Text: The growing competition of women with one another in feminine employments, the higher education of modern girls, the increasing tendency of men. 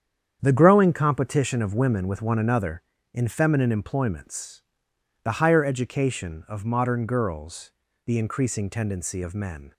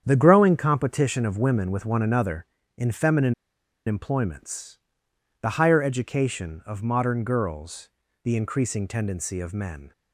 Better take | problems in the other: first | starts louder than the rest; strong; until 1.0 s; 8.5 dB; strong in the first // pauses between "feminine" and "employments"; noticeable; at 3.3 s; 0.53 s long

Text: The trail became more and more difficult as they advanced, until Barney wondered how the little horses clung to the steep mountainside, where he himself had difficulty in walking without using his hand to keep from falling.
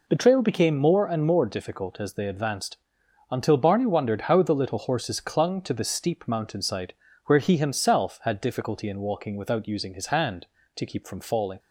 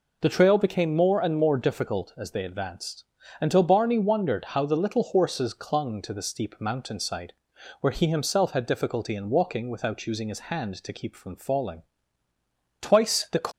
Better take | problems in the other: first | goes on to say "Twice the"; noticeable; from 12.7 s on; 0.68 s long

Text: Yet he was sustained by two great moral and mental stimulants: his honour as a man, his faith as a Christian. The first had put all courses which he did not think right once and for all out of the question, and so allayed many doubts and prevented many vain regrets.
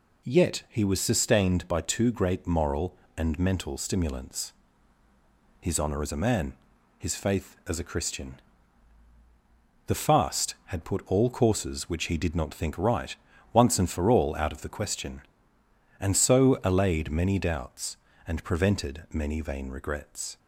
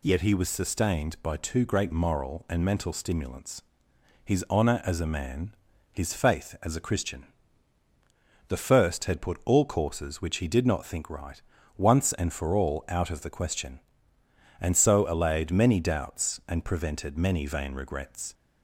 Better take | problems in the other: second | says "fast" for "first"; at 9.9 s // pauses between "right" and "once"; at 13.1 s; 0.38 s long; slight in the second

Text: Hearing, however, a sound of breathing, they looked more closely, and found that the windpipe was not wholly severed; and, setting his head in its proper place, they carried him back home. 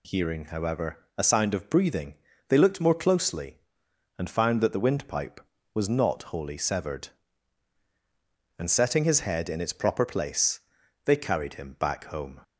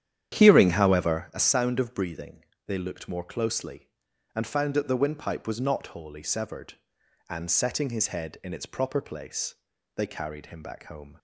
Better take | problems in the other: first | starts louder than the rest; strong; until 1.3 s; 10 dB

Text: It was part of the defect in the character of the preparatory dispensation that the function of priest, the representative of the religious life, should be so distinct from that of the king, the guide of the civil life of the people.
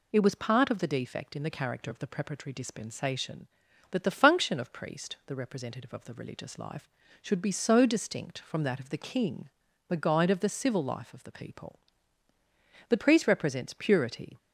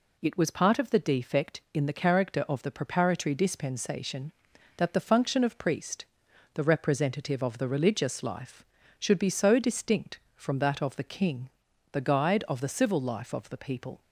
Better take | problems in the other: second | goes on to say "The priest represents purity"; from 12.8 s on; 1.4 s long

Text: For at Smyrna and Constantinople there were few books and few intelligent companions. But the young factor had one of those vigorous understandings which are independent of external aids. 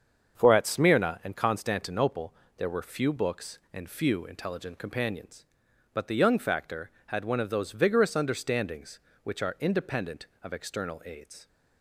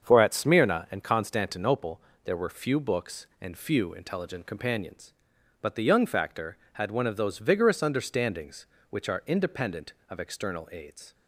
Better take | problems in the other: neither | starts louder than the rest; the same in both // pauses between "Constantinople" and "there"; slight; the same in both

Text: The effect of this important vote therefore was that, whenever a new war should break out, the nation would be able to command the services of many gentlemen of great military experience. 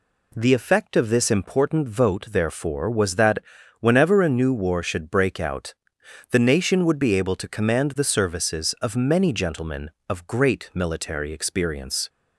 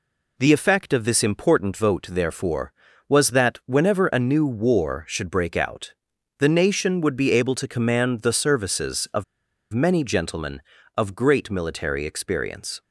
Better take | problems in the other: first | pauses between "of" and "many"; noticeable; at 9.2 s; 0.49 s long

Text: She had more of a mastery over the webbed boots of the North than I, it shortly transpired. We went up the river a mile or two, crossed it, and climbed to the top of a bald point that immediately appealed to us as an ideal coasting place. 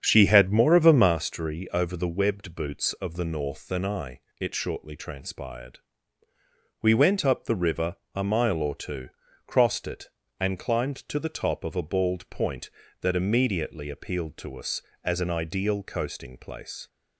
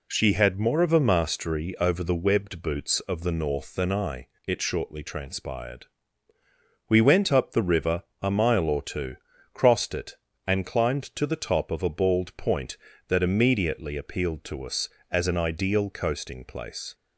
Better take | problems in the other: second | starts louder than the rest; strong; until 1.1 s; 8 dB // pauses between "river" and "a"; slight; at 7.9 s; 0.20 s long; slight in the second

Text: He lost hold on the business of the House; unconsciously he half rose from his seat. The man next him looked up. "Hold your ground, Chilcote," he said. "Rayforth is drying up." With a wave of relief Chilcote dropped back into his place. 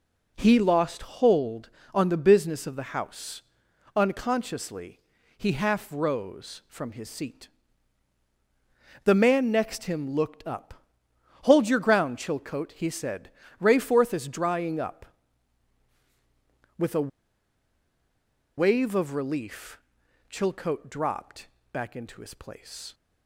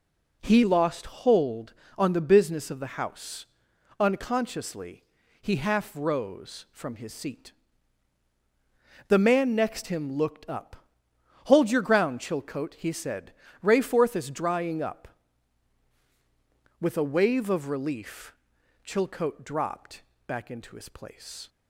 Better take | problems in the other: second | pauses between "unconsciously" and "he"; at 4.9 s; 0.38 s long; also in the second // pauses between "a" and "wave"; strong; at 17.0 s; 1.4 s long // pauses between "relief" and "Chilcote"; noticeable; at 19.7 s; 0.50 s long; noticeable in the second // pauses between "dropped" and "back"; slight; at 21.4 s; 0.24 s long; slight in the second

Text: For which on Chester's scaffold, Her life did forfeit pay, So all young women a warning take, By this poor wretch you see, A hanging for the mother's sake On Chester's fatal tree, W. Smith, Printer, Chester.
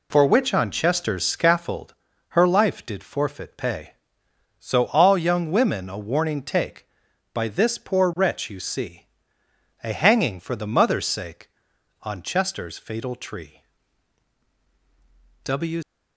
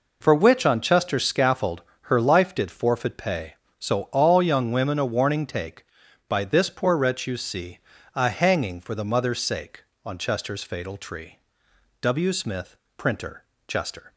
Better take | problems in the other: second | stops before "Smith Printer Chester"; at 15.8 s

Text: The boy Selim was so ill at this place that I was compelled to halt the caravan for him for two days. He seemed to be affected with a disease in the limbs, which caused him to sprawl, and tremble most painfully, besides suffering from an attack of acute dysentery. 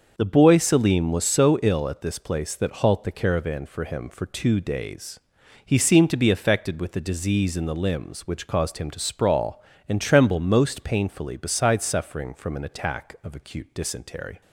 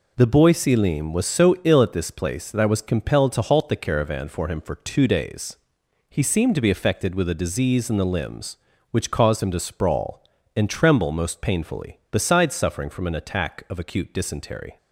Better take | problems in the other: second | starts louder than the rest; until 1.1 s; 6 dB // skips "I was compelled to"; at 2.8 s

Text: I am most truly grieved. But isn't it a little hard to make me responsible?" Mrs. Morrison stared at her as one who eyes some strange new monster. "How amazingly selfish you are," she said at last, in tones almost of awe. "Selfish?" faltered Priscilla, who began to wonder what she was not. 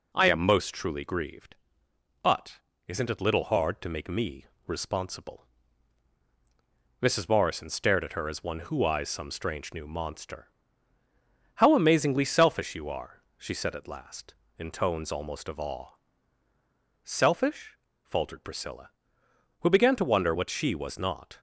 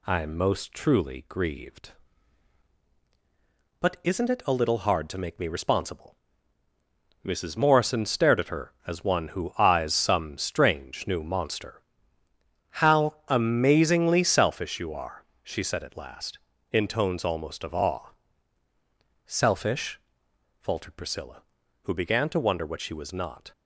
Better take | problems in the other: second | pauses between "But" and "isn't"; slight; at 2.5 s; 0.30 s long // skips "a"; at 3.2 s // pauses between "me" and "responsible"; slight; at 4.4 s; 0.20 s long

